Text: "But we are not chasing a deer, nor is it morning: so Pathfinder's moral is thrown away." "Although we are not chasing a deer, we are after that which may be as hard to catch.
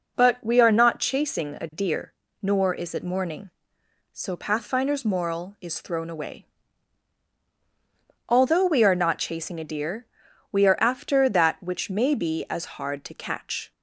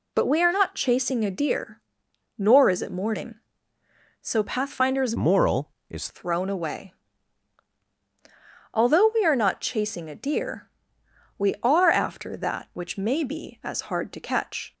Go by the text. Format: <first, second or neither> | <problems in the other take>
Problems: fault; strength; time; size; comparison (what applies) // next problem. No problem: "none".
first | changes voice from "moral" to "is"; from 5.1 to 6.0 s; 0.9 s long